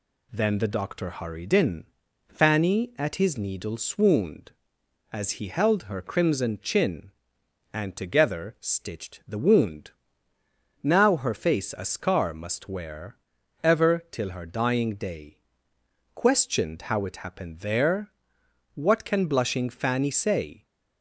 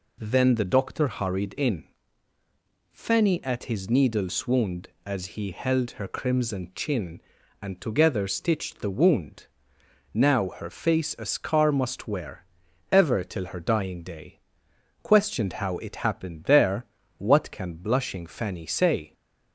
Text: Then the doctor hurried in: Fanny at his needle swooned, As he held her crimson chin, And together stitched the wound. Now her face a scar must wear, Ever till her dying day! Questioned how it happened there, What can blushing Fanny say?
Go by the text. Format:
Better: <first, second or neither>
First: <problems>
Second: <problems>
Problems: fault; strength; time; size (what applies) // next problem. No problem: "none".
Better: neither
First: none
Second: none